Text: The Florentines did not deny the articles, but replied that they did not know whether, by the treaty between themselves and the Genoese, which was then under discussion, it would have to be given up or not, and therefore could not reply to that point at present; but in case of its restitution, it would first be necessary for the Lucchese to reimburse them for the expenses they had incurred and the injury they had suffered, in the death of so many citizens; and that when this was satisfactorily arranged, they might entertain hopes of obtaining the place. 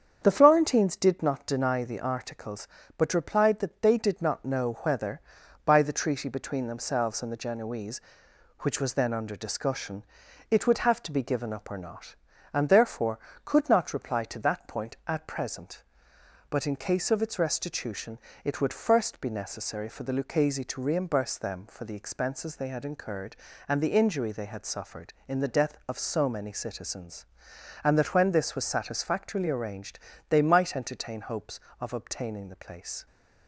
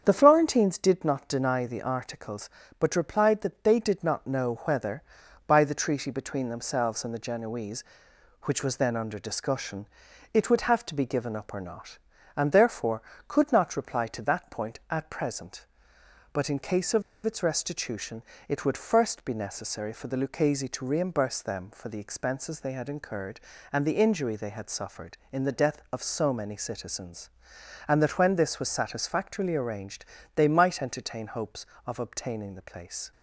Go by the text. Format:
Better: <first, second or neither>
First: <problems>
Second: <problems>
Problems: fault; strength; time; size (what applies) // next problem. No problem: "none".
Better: first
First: starts louder than the rest; strong; until 1.2 s; 7.5 dB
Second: starts louder than the rest; strong; until 1.0 s; 7.5 dB // pauses between "of" and "its"; slight; at 17.0 s; 0.23 s long